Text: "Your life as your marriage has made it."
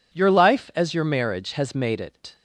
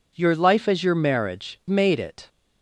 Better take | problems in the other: first | skips "has"; at 1.6 s

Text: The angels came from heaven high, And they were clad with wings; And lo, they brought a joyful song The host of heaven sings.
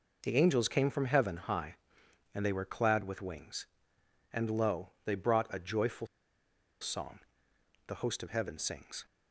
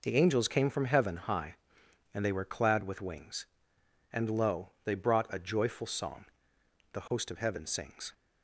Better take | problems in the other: second | pauses between "joyful" and "song"; noticeable; at 6.0 s; 0.74 s long // pauses between "song" and "The"; noticeable; at 7.1 s; 0.68 s long; noticeable in the second

